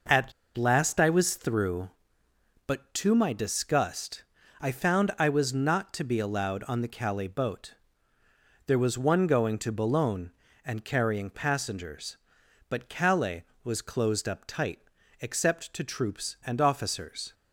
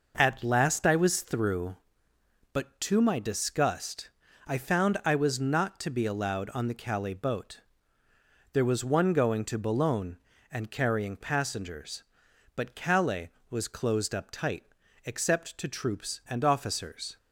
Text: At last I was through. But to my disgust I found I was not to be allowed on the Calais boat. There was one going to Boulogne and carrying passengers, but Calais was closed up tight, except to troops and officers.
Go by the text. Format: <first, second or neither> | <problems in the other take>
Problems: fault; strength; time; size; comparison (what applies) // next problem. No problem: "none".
second | pauses between "At" and "last"; slight; at 0.3 s; 0.23 s long // pauses between "disgust" and "I"; at 4.2 s; 0.38 s long; also in the second